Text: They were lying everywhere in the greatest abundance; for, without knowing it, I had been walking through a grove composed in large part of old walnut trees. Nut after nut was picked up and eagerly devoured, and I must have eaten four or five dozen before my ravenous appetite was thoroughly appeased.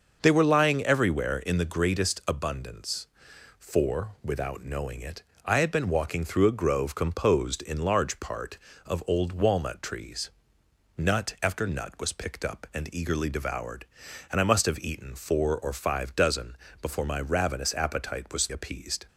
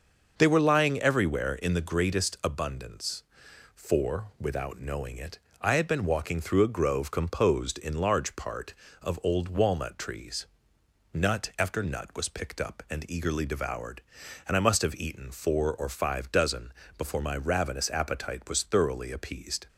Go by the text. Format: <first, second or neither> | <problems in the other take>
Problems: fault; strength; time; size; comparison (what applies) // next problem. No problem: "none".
second | starts louder than the rest; until 1.2 s; 6.5 dB; also in the second // pauses between "dozen" and "before"; slight; at 16.5 s; 0.24 s long; slight in the second // skips "thoroughly"; at 18.4 s